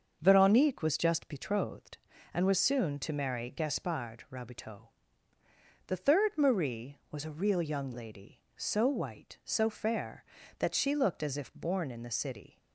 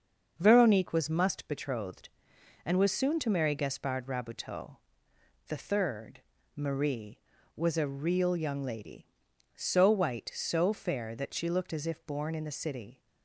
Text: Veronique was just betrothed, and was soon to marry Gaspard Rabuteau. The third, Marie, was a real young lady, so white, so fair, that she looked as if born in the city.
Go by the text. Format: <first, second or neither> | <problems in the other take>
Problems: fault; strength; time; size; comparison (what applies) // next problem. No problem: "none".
first | starts louder than the rest; until 1.3 s; 6.5 dB; also in the first // says "must" for "just"; at 1.0 s